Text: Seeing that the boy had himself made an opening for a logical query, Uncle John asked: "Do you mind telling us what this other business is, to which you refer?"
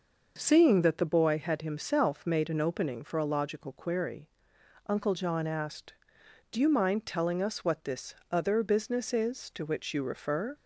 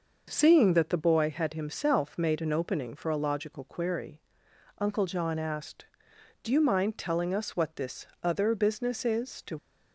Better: first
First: pauses between "this" and "other"; slight; at 8.1 s; 0.18 s long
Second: pauses between "this" and "other"; slight; at 8.0 s; 0.18 s long // stops before "which you refer"; at 9.5 s

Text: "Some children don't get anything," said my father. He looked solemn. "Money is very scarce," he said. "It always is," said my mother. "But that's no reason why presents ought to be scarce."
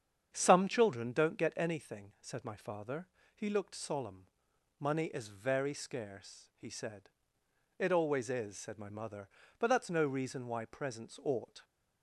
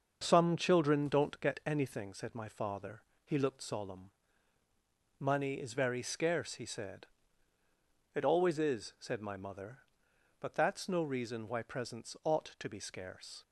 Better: second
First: starts louder than the rest; strong; until 1.3 s; 8 dB // stops before "to be scarce"; at 11.6 s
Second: starts louder than the rest; until 1.2 s; 6.5 dB

